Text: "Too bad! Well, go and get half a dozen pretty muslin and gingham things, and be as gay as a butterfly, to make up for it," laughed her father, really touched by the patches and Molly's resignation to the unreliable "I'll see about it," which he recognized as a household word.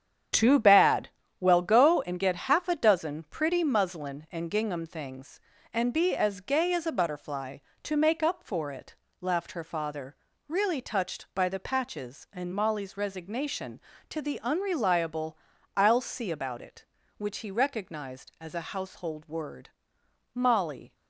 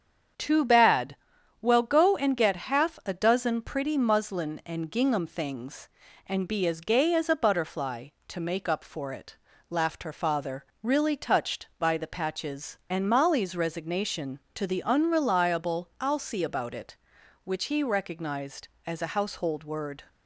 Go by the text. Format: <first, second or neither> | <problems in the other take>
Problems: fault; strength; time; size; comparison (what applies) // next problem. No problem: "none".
second | starts louder than the rest; strong; until 1.6 s; 8.5 dB; strong in the second // pauses between "unreliable" and "I'll"; at 15.3 s; 0.40 s long // goes on to say "Molly"; noticeable; from 20.3 s on; 0.62 s long